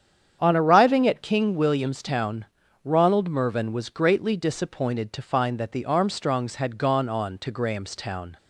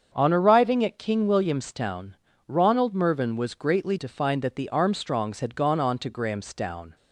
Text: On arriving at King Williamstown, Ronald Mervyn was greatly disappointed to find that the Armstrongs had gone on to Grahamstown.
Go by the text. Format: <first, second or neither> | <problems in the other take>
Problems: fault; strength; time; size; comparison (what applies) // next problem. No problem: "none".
first | starts louder than the rest; strong; until 1.1 s; 7 dB; strong in the first // skips "disappointed"; at 3.9 s